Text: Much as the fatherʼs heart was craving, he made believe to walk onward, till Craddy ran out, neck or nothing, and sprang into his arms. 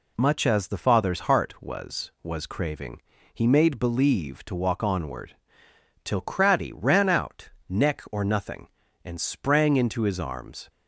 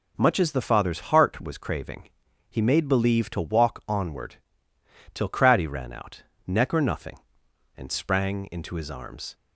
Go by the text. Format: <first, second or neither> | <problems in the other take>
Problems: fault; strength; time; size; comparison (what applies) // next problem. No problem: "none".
second | says "was" twice; at 2.2 s